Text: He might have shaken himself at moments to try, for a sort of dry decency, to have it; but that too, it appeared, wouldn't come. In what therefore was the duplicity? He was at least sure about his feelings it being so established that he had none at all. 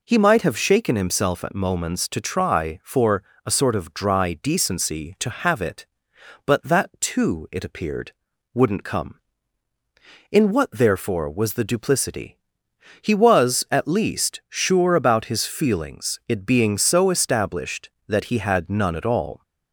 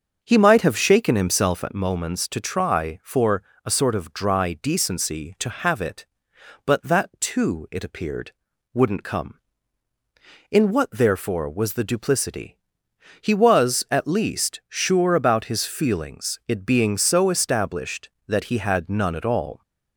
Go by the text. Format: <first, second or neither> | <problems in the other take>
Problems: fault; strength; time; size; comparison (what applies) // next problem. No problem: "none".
first | starts louder than the rest; until 1.9 s; 6.5 dB // pauses between "for" and "a"; slight; at 3.4 s; 0.24 s long; slight in the first